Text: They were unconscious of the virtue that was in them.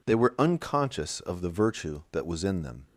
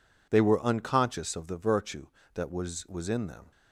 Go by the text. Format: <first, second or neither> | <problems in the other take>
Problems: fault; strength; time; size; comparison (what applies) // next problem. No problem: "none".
first | says "was" twice; at 2.8 s